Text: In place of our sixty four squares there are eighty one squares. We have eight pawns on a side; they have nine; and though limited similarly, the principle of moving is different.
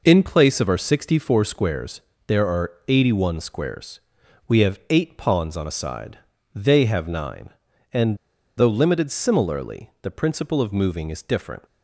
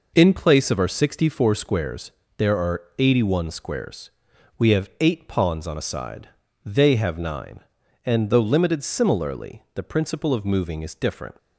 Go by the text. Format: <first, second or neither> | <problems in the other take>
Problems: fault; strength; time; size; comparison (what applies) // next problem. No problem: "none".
second | pauses between "squares" and "there"; slight; at 2.0 s; 0.26 s long; slight in the second // pauses between "are" and "eighty"; slight; at 2.7 s; 0.16 s long; slight in the second // pauses between "and" and "though"; at 8.1 s; 0.40 s long